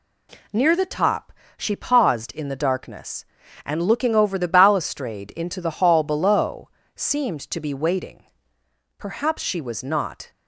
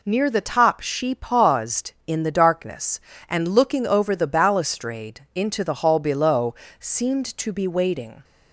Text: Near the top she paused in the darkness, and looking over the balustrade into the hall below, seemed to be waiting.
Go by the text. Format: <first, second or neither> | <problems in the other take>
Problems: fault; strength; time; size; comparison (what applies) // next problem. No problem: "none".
second | pauses between "top" and "she"; slight; at 1.3 s; 0.24 s long // goes on to say "Perhaps she was not"; from 8.9 s on; 1.3 s long